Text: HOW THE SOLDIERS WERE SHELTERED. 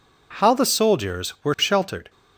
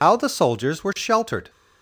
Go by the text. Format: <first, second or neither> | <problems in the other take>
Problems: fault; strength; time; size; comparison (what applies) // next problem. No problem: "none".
first | loses the start of "HOW"; at 0.0 s; 65 ms